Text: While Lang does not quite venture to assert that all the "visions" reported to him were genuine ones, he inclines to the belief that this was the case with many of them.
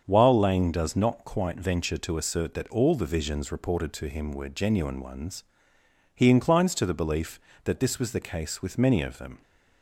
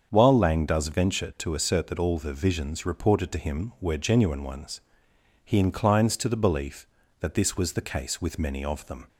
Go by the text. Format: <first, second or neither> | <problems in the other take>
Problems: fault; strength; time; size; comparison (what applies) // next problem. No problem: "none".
first | starts louder than the rest; until 1.1 s; 7 dB; also in the first // skips "not quite"; at 0.8 s